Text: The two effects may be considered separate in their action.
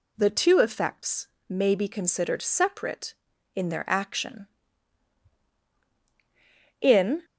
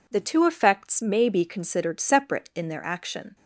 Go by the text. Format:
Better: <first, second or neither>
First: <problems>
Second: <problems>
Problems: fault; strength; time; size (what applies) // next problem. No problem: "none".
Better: second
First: pauses between "effects" and "may"; slight; at 1.2 s; 0.22 s long // goes on to say "In"; slight; from 6.8 s on; 0.44 s long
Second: none